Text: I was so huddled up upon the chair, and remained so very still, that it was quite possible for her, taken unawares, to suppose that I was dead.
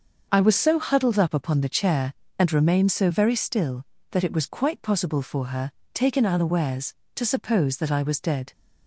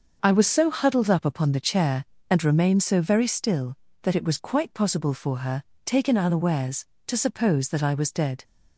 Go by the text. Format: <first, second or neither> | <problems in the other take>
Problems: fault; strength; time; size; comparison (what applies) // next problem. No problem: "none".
neither | starts louder than the rest; the same in both